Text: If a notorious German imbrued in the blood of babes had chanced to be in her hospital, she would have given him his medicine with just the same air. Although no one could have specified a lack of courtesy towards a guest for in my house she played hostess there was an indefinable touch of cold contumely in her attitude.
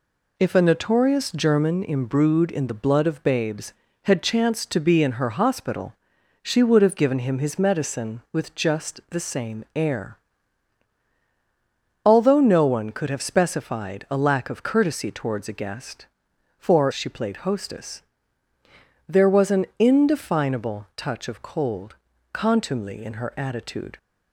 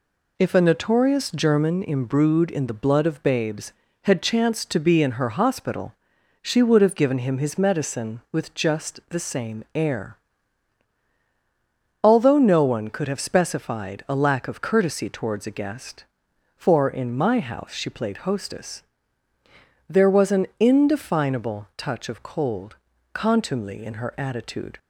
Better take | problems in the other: second | skips "in my house"; at 16.9 s // pauses between "hostess" and "there"; at 18.0 s; 1.0 s long; also in the second // pauses between "cold" and "contumely"; slight; at 21.9 s; 0.36 s long; slight in the second

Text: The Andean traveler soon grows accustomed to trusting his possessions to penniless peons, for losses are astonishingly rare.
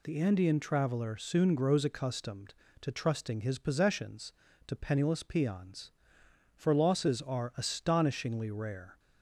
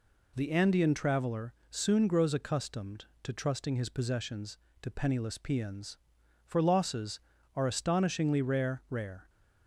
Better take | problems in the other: first | pauses between "traveler" and "soon"; slight; at 1.5 s; 0.16 s long // says "rare" twice; at 8.8 s

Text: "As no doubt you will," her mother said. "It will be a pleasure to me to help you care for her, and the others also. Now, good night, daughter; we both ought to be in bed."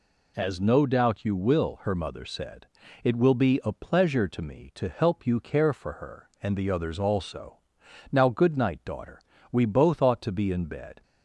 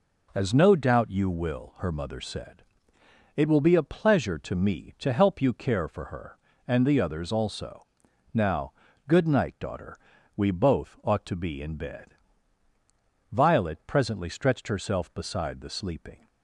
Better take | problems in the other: first | goes on to say "Violet presently stretched herself beside the sleeping"; strong; from 13.3 s on; 2.9 s long

